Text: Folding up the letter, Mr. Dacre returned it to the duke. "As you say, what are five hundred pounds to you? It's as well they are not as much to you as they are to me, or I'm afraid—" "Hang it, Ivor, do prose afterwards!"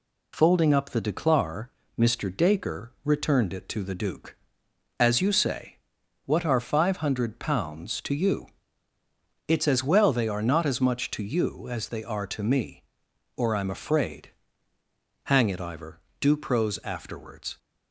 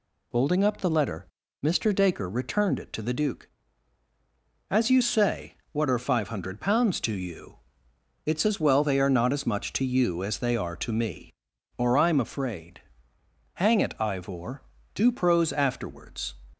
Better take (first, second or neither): second